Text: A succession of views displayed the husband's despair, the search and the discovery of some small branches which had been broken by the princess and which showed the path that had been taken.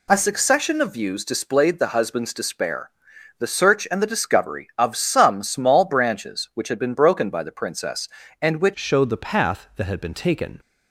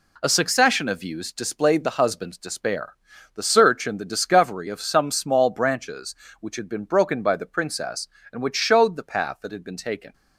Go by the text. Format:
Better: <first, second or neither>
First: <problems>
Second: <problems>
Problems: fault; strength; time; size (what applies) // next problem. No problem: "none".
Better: second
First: changes voice at "showed"; from 8.7 s on; 1.8 s long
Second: none